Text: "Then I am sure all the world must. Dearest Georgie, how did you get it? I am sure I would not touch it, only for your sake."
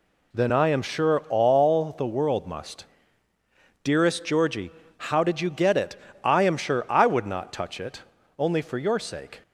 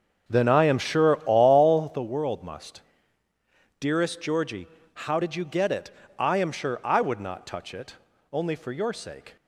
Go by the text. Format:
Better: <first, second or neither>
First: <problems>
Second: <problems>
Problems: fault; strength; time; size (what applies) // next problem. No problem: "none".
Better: first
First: none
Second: starts louder than the rest; strong; until 2.0 s; 7 dB